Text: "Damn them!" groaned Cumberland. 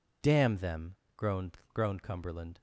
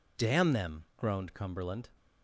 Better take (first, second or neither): second